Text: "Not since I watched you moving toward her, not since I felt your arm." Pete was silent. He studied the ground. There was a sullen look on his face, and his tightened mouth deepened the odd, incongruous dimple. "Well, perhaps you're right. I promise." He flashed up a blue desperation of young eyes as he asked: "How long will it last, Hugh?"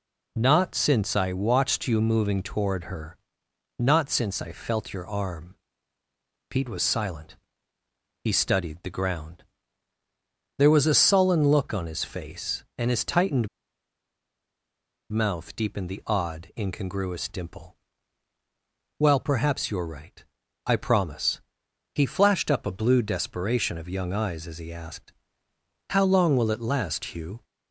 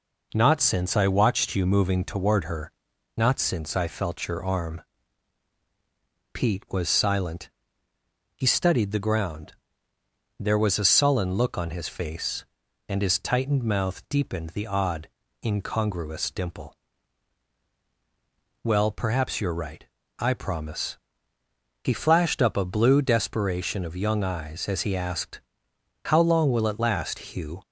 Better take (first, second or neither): second